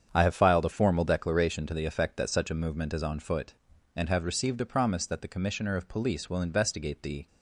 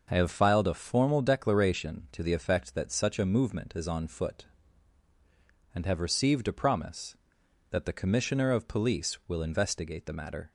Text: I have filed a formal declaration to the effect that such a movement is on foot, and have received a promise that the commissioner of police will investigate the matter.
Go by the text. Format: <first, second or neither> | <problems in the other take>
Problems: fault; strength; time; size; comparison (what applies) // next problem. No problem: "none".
second | starts louder than the rest; strong; until 1.1 s; 8 dB // stops before "matter"; at 7.2 s